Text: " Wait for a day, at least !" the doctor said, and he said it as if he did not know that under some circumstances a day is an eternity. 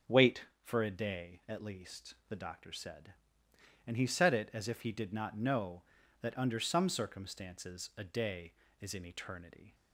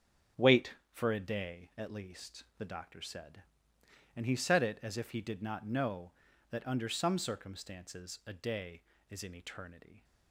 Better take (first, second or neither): first